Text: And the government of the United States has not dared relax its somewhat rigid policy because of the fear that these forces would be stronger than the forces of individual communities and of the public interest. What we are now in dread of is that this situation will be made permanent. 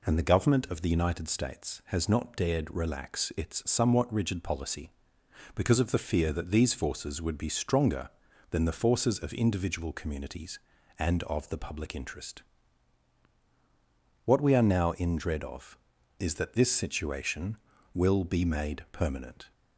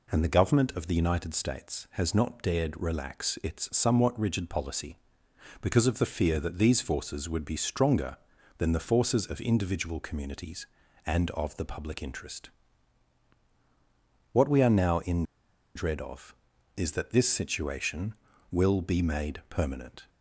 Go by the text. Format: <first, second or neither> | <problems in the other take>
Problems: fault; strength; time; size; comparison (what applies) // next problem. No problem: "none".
first | pauses between "in" and "dread"; noticeable; at 15.2 s; 0.52 s long